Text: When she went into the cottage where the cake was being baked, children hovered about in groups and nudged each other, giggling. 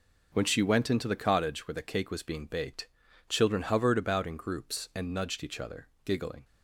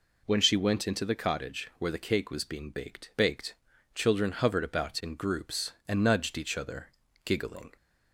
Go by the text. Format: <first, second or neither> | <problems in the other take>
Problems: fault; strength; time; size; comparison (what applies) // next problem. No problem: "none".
first | says "baked" twice; at 3.1 s